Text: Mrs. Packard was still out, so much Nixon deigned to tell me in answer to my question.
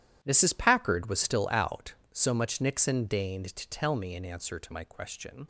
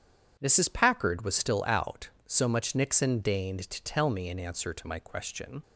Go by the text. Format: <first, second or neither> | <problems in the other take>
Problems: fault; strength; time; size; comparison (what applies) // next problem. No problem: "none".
second | gets quieter; strong; throughout; 14 dB // starts louder than the rest; strong; until 1.2 s; 11.5 dB; strong in the second